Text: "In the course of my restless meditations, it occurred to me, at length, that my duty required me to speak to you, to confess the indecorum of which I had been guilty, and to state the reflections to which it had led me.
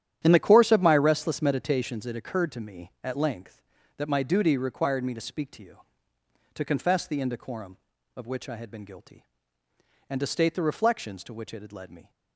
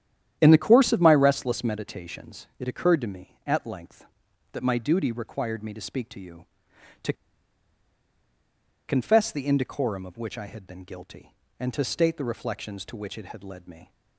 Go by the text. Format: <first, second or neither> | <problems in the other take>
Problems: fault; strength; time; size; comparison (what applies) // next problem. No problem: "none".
first | starts louder than the rest; strong; until 1.4 s; 10.5 dB; strong in the first // pauses between "to" and "confess"; strong; at 7.1 s; 1.7 s long